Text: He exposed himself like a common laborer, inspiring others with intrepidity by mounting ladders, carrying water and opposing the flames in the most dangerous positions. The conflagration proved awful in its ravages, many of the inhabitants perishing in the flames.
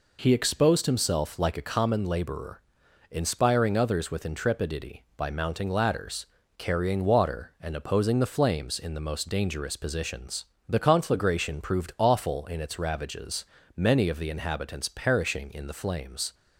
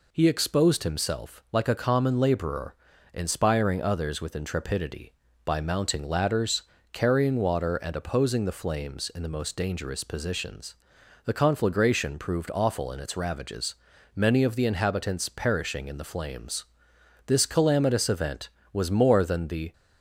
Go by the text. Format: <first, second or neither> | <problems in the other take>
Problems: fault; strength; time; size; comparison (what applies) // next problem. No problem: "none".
first | goes on to say "This calamitous event was more than the"; strong; from 17.2 s on; 2.4 s long